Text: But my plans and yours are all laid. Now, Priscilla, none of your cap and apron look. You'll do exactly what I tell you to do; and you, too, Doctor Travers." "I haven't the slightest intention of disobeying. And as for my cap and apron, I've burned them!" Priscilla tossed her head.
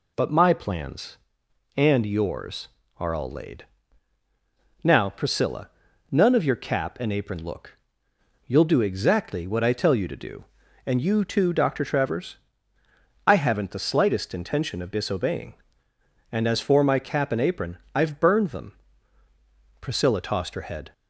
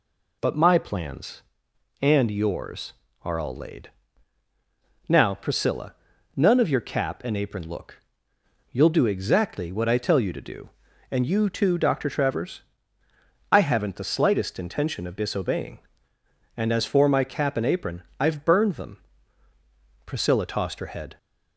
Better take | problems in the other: neither | none

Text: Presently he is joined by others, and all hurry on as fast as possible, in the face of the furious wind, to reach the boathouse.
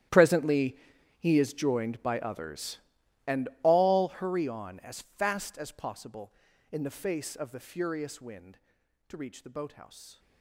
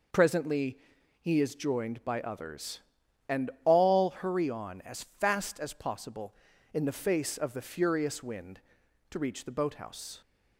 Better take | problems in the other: second | gets quieter; strong; throughout; 18.5 dB // pauses between "Presently" and "he"; at 0.7 s; 0.42 s long; also in the second

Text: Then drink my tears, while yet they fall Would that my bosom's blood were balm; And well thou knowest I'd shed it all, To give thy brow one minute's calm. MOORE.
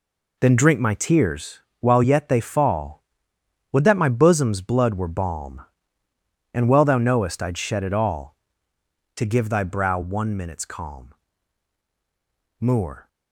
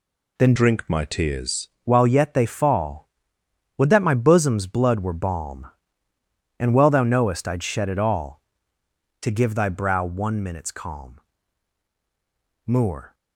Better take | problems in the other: first | changes voice from "drink" to "tears"; from 0.5 to 1.6 s; 1.1 s long

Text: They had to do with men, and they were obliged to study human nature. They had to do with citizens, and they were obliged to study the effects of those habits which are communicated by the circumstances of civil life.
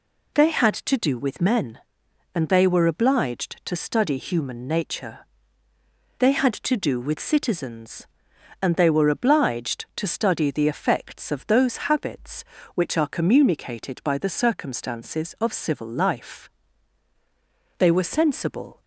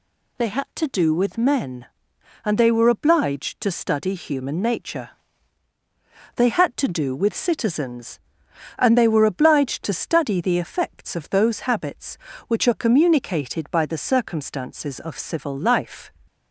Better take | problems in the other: second | goes on to say "They were sensible"; noticeable; from 17.7 s on; 1.0 s long

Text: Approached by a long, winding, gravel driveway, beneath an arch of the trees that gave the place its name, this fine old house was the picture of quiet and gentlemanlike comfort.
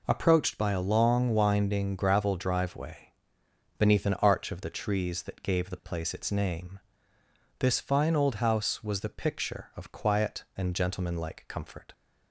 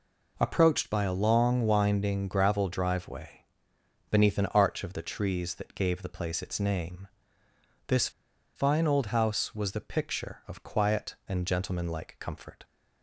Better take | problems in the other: first | pauses between "this" and "fine"; noticeable; at 8.0 s; 0.46 s long

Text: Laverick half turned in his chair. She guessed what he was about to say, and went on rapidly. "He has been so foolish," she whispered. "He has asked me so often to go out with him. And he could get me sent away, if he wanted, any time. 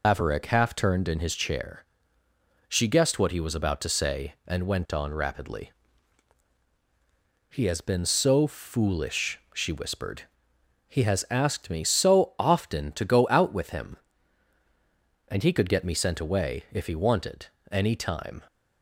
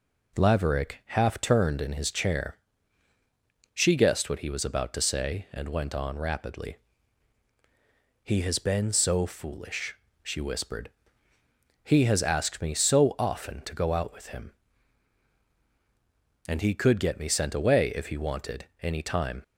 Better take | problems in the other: second | loses the start of "Laverick"; at 0.0 s; 125 ms

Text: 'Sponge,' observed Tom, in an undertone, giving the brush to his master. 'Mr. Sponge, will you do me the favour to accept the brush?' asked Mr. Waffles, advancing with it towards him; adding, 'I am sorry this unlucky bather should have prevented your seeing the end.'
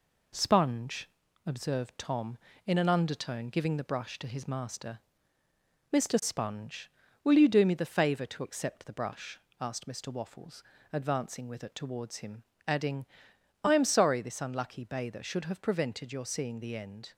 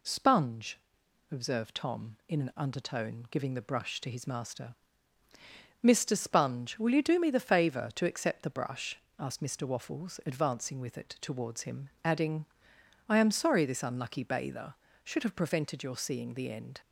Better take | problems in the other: second | gets quieter; slight; throughout; 3 dB

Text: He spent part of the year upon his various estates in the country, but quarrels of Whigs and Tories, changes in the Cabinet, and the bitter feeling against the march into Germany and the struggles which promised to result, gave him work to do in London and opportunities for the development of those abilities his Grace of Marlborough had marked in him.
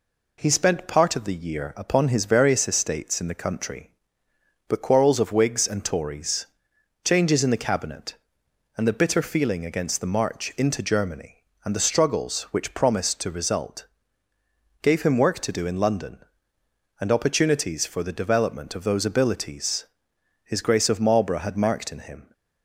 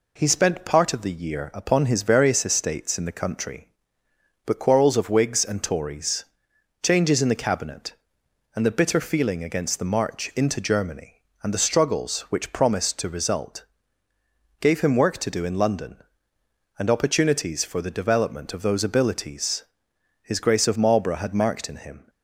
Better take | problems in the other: neither | pauses between "abilities" and "his"; noticeable; the same in both

